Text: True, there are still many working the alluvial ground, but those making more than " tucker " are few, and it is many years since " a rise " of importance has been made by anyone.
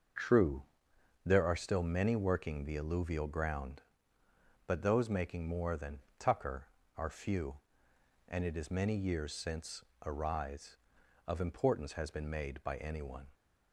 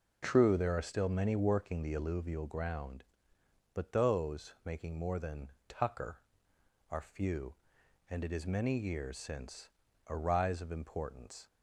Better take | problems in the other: first | starts louder than the rest; until 1.2 s; 6.5 dB; also in the first // stops before "has been made by anyone"; at 11.4 s

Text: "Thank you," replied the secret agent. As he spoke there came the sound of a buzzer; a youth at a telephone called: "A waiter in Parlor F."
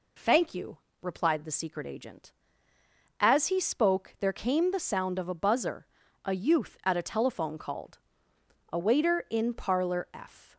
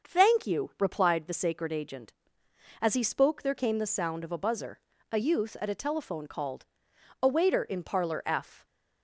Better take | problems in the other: first | starts louder than the rest; until 1.1 s; 6.5 dB // says "sacred" for "secret"; at 1.3 s

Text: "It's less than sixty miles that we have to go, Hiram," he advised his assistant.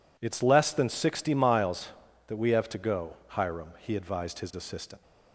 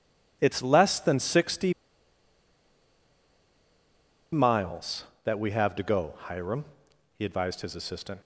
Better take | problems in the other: first | pauses between "sixty" and "miles"; strong; at 1.7 s; 2.6 s long

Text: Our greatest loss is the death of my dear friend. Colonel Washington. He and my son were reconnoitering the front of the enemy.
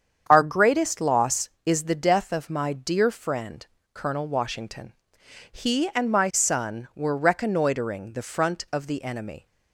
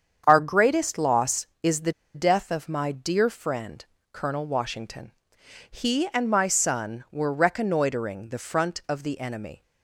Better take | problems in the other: first | starts louder than the rest; strong; until 1.2 s; 8 dB; strong in the first // pauses between "the" and "death"; slight; at 1.9 s; 0.21 s long

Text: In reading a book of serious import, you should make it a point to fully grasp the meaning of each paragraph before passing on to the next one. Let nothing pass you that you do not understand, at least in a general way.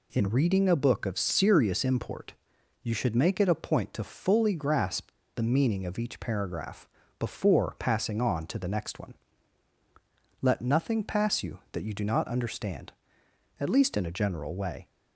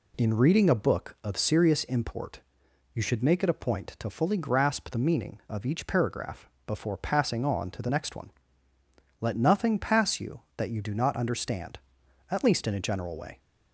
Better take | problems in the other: second | pauses between "grasp" and "the"; slight; at 5.0 s; 0.26 s long // pauses between "paragraph" and "before"; slight; at 6.8 s; 0.32 s long; slight in the second

